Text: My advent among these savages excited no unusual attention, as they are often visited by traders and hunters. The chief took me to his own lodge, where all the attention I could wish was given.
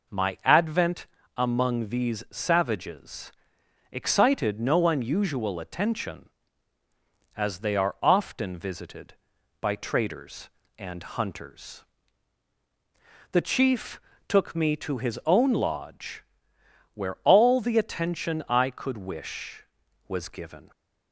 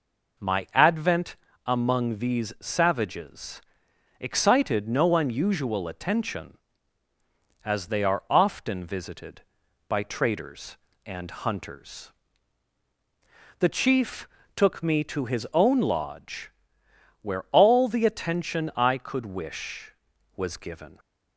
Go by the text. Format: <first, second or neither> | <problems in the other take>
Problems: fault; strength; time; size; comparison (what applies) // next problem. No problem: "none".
neither | pauses between "advent" and "among"; slight; the same in both // pauses between "savages" and "excited"; noticeable; the same in both // pauses between "chief" and "took"; slight; the same in both